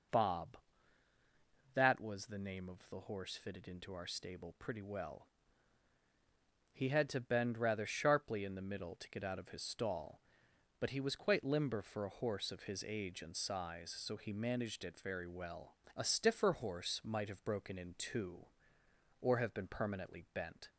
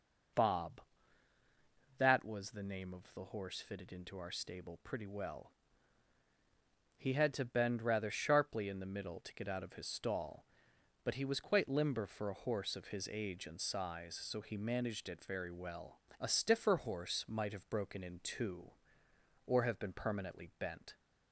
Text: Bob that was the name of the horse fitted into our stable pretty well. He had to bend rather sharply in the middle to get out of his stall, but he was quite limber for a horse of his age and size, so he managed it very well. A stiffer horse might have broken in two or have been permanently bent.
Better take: neither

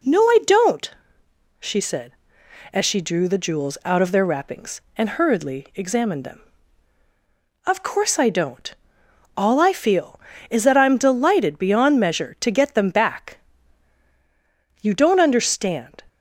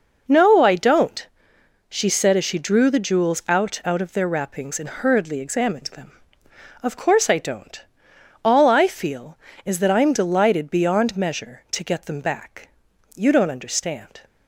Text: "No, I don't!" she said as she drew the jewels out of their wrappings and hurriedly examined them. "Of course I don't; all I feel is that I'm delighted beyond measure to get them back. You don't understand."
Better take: first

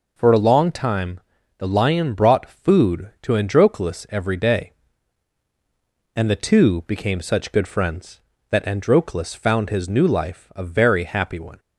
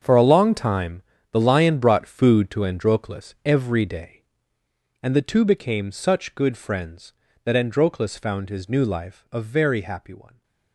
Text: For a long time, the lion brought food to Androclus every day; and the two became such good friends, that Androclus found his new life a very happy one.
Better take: first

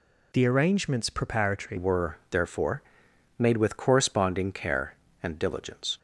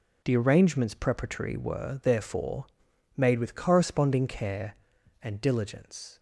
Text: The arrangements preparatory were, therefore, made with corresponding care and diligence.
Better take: second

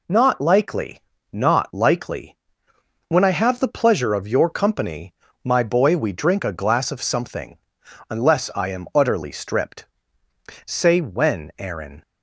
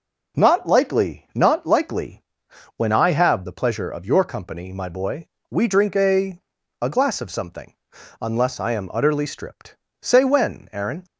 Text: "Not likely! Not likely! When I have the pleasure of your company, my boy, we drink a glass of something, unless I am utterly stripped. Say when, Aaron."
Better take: first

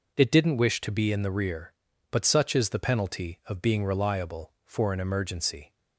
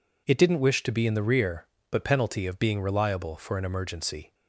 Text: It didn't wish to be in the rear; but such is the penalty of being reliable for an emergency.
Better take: first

